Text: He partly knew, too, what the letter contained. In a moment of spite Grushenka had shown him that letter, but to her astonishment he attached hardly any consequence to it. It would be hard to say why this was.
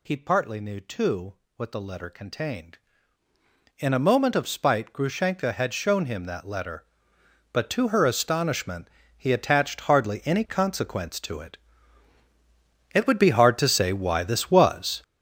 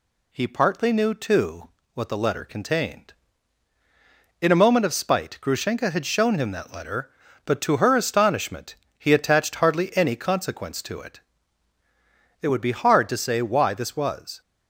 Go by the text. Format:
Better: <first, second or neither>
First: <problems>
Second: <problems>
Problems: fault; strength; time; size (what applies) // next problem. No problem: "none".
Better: second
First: gets louder; strong; throughout; 10.5 dB // pauses between "astonishment" and "he"; slight; at 8.8 s; 0.28 s long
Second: pauses between "astonishment" and "he"; slight; at 8.7 s; 0.22 s long